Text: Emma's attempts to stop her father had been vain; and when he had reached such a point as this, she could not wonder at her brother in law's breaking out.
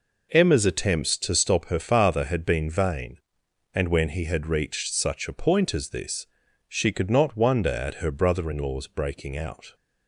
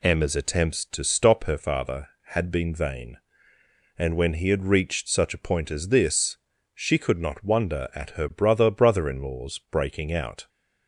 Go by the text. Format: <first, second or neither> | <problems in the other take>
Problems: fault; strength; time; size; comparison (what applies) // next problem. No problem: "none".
first | says "brother" twice; at 8.6 s